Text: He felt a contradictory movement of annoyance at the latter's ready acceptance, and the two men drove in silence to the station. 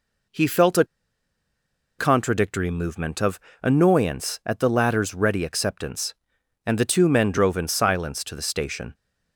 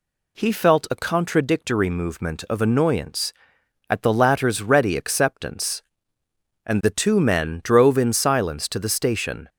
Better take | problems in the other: second | pauses between "a" and "contradictory"; at 0.8 s; 1.1 s long // pauses between "of" and "annoyance"; slight; at 3.3 s; 0.22 s long

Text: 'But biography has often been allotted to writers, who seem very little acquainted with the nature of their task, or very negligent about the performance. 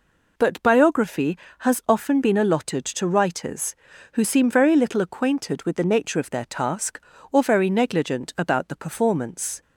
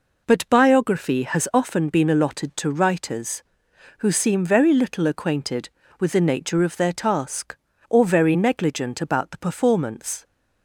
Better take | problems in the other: neither | none

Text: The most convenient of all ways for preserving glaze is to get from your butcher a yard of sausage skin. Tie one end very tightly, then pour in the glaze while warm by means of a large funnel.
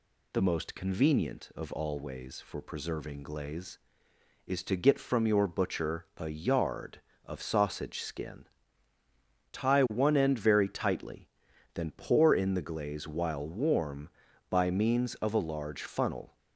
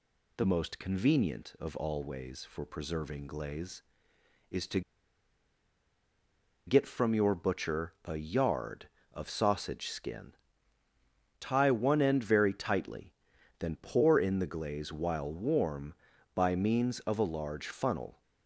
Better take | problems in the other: first | pauses between "to" and "get"; strong; at 4.8 s; 1.8 s long

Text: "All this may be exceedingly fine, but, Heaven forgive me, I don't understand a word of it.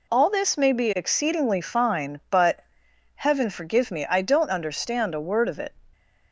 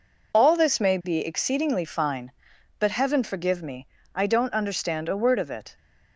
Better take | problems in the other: neither | none

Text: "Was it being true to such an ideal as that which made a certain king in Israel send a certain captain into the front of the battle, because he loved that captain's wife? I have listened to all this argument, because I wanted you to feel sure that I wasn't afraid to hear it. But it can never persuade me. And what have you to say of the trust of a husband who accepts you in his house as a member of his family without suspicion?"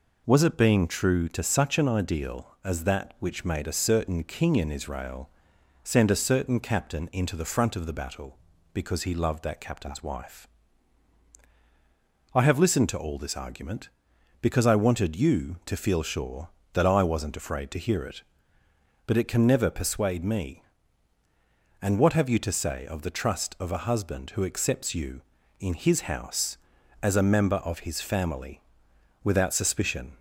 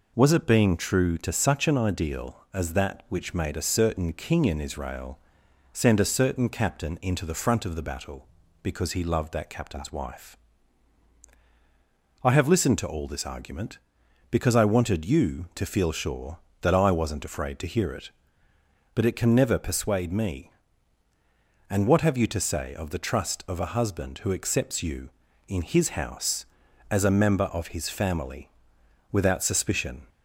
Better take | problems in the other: neither | pauses between "Israel" and "send"; noticeable; the same in both // pauses between "family" and "without"; noticeable; the same in both

